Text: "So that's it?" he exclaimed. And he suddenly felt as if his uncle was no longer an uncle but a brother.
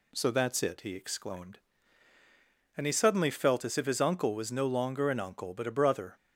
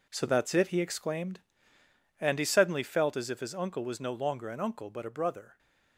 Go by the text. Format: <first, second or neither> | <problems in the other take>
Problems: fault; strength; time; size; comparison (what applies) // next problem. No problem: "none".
first | gets quieter; strong; throughout; 9 dB